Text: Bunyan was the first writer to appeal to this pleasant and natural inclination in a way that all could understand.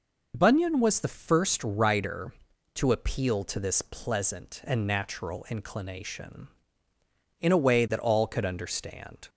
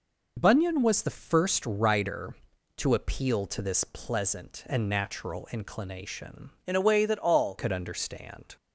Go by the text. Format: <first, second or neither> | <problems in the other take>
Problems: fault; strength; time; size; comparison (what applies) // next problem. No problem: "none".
first | changes voice from "in" to "all"; from 6.6 to 7.5 s; 0.9 s long